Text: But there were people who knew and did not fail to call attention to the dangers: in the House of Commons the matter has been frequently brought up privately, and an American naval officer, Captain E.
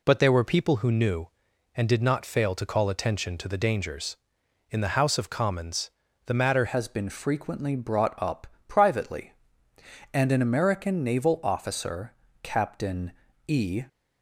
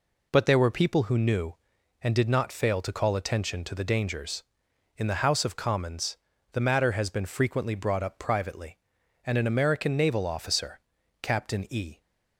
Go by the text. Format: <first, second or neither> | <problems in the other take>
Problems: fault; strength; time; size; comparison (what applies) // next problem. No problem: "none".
second | pauses between "Commons" and "the"; slight; at 5.9 s; 0.36 s long; slight in the second // changes voice at "has"; from 6.6 s on; 7.2 s long // pauses between "up" and "privately"; slight; at 8.4 s; 0.22 s long // pauses between "Captain" and "E"; slight; at 13.1 s; 0.34 s long